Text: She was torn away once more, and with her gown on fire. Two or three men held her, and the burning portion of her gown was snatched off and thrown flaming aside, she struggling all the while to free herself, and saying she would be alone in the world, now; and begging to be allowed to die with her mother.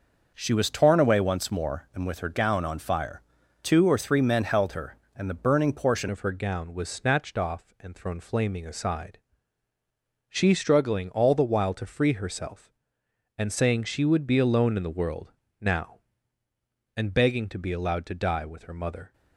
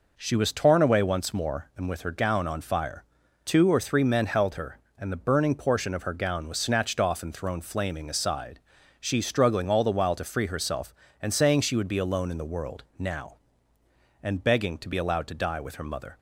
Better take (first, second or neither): second